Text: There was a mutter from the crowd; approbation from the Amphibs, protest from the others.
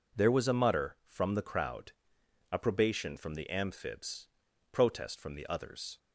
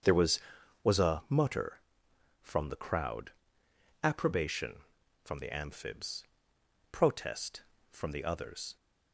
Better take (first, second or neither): first